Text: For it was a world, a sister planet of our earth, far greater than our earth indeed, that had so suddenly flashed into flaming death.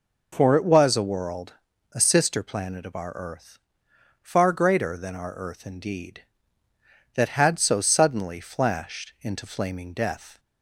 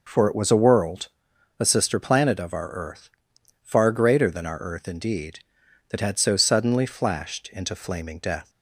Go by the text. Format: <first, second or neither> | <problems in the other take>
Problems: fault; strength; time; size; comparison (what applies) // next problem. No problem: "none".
neither | none